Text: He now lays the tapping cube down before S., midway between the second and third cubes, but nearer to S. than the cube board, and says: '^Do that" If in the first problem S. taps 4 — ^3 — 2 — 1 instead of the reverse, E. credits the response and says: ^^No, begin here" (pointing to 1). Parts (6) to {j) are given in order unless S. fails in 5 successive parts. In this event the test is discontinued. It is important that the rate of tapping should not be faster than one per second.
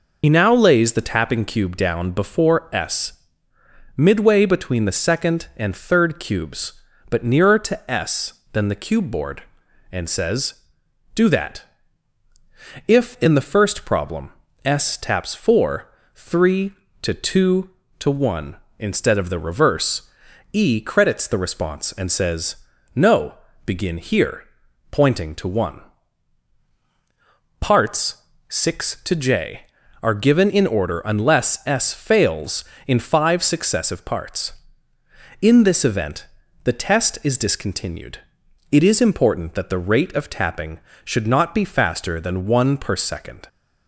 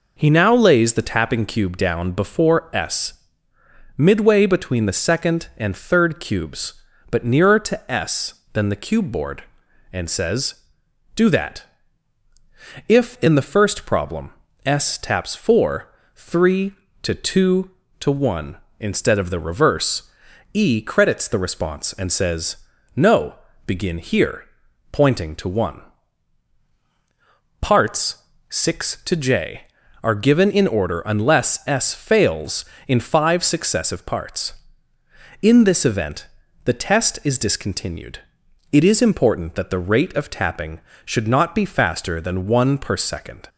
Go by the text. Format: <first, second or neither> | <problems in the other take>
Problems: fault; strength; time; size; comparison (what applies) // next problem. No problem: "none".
second | loses the start of "He"; at 0.2 s; 70 ms // pauses between "that" and "If"; at 11.6 s; 1.2 s long; also in the second // pauses between "problem" and "S"; slight; at 14.3 s; 0.34 s long; slight in the second // pauses between "event" and "the"; at 36.2 s; 0.38 s long; also in the second